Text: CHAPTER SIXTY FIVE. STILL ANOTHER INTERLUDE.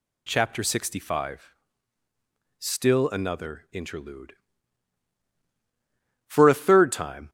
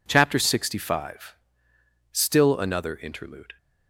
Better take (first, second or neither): second